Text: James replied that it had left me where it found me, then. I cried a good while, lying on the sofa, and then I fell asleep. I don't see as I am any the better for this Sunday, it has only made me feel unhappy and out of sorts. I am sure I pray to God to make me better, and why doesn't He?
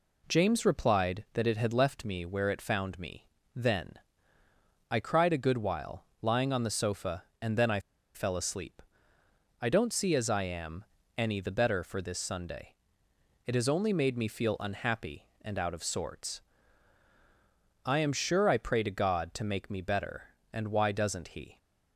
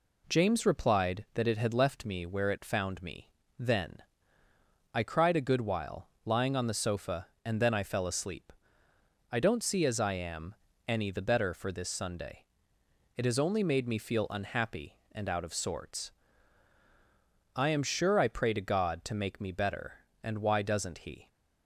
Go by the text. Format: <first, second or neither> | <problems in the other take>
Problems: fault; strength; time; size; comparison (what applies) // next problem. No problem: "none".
second | pauses between "I" and "fell"; slight; at 7.7 s; 0.36 s long // pauses between "am" and "any"; slight; at 10.8 s; 0.32 s long; slight in the second